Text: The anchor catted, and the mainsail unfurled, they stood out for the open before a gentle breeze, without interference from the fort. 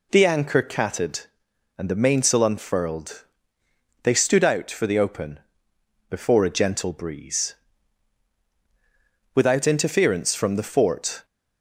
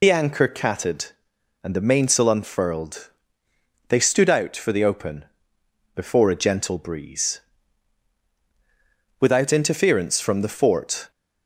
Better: first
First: pauses between "open" and "before"; noticeable; at 5.4 s; 0.68 s long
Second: loses the start of "The"; at 0.0 s; 60 ms // pauses between "open" and "before"; noticeable; at 5.2 s; 0.68 s long

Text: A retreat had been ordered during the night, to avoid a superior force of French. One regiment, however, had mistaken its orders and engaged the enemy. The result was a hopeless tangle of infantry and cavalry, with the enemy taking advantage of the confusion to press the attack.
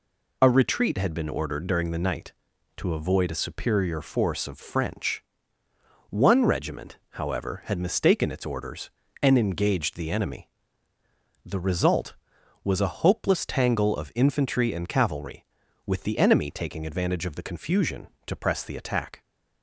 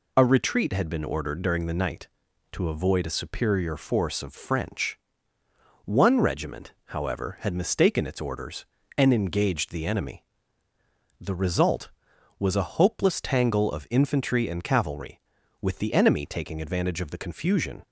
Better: first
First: none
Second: stops before "to press the attack"; at 17.8 s

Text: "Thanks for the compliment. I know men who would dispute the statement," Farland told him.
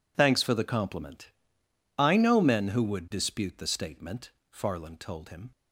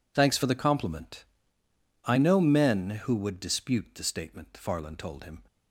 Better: neither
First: none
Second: none

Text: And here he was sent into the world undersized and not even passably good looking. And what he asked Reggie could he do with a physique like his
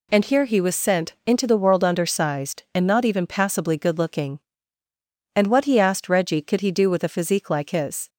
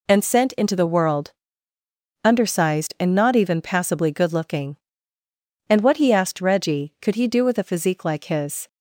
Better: first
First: none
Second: skips "here he was"; at 0.2 s // pauses between "world" and "undersized"; noticeable; at 1.3 s; 0.92 s long

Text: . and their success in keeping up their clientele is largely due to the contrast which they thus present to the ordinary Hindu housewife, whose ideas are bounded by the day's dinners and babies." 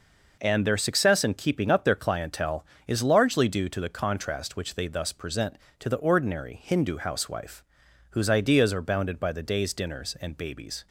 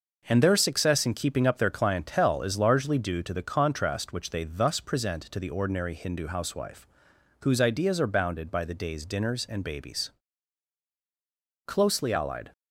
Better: first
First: none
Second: goes on to say "Closely allied"; noticeable; from 11.6 s on; 0.86 s long

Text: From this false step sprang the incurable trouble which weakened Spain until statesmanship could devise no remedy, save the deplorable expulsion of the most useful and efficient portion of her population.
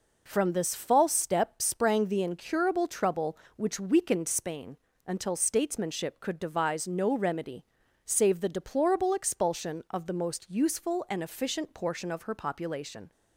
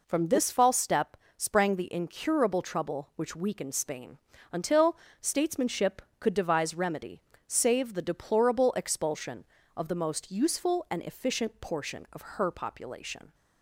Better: first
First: pauses between "Spain" and "until"; slight; at 4.7 s; 0.30 s long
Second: pauses between "step" and "sprang"; slight; at 1.1 s; 0.20 s long // pauses between "Spain" and "until"; slight; at 4.1 s; 0.34 s long // pauses between "until" and "statesmanship"; slight; at 4.9 s; 0.24 s long // skips "no"; at 6.7 s

